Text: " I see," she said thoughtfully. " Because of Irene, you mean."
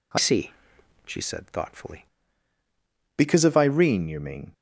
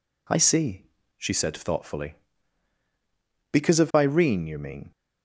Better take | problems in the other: second | changes voice from "see" to "thoughtfully"; from 0.1 to 2.0 s; 1.9 s long

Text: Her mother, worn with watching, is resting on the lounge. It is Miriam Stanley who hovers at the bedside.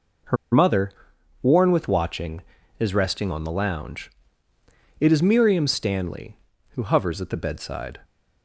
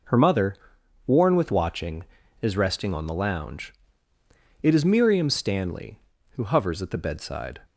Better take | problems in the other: second | pauses between "Her" and "mother"; slight; at 0.3 s; 0.17 s long

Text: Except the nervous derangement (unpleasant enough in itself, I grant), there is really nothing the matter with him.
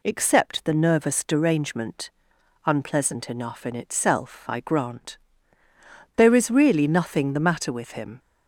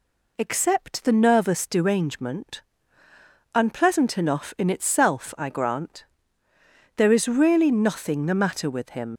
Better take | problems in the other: first | leaves "him" unfinished; at 9.1 s; 60 ms

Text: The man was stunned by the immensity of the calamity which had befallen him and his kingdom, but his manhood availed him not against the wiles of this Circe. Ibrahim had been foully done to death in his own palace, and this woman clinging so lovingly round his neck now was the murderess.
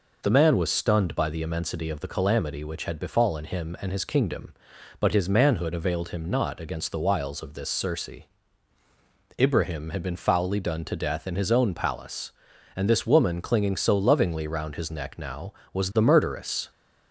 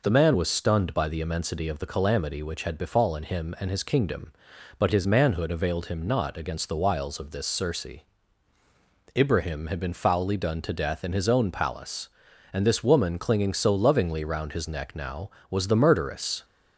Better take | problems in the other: neither | none

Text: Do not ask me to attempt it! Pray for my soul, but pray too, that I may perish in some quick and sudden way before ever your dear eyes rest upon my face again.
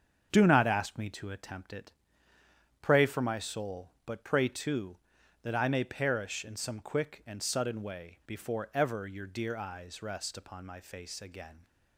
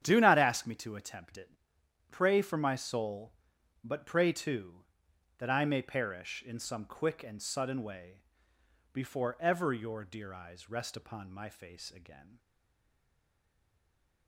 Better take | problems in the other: first | starts louder than the rest; strong; until 1.0 s; 9 dB; strong in the first // pauses between "way" and "before"; noticeable; at 8.2 s; 0.72 s long // stays silent after the last word; noticeable; from 12.3 s on; 1.9 s long

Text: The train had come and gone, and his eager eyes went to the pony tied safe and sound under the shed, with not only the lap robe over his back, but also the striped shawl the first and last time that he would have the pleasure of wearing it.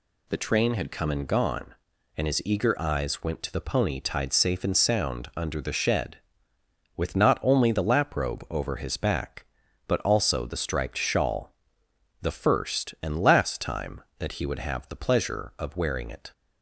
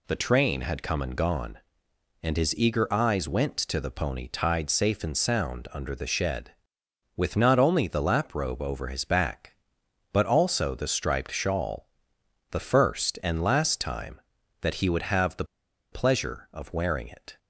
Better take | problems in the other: first | pauses between "shawl" and "the"; noticeable; at 11.8 s; 0.64 s long; noticeable in the first // pauses between "the" and "pleasure"; noticeable; at 15.4 s; 0.47 s long

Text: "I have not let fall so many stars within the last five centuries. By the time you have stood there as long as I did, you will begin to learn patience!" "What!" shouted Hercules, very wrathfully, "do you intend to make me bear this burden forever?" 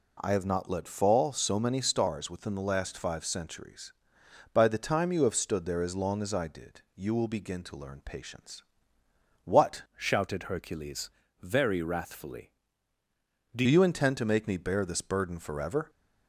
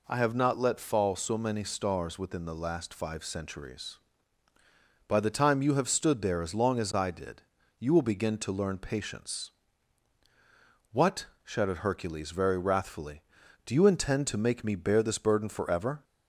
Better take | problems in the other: second | changes voice from "shouted" to "do"; from 9.9 to 13.6 s; 3.7 s long

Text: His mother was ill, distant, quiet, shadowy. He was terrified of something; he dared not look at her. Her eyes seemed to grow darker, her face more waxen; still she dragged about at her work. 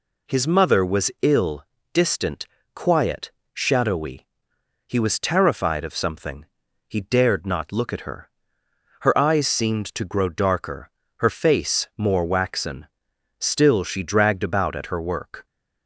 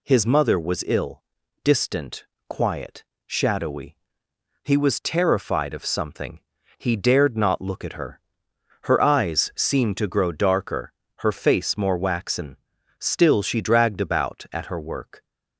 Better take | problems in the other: neither | none

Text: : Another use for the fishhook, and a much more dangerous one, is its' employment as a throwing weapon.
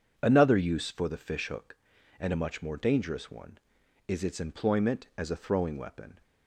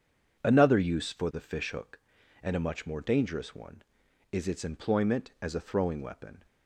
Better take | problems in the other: neither | starts louder than the rest; strong; the same in both

